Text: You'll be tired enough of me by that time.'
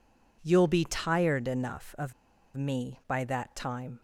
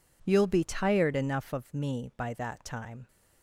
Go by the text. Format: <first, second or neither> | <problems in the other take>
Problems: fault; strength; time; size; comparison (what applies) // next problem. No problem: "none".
second | pauses between "of" and "me"; at 2.1 s; 0.43 s long